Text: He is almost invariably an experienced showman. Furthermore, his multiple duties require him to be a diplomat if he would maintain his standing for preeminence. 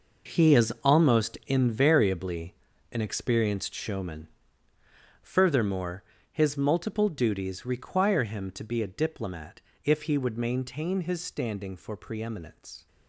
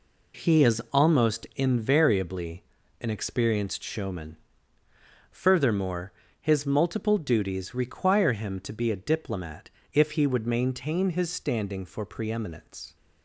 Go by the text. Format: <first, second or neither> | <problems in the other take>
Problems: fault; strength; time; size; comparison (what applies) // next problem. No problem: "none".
second | gets quieter; strong; throughout; 12 dB // pauses between "invariably" and "an"; slight; at 2.5 s; 0.34 s long; slight in the second // pauses between "diplomat" and "if"; slight; at 9.6 s; 0.24 s long; slight in the second